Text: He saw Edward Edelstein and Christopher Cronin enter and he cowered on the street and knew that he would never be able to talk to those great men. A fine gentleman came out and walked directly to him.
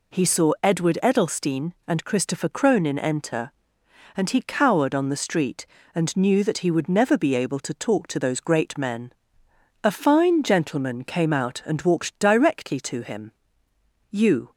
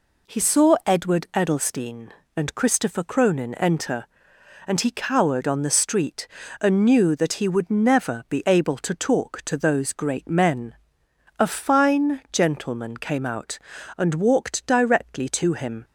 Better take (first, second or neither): second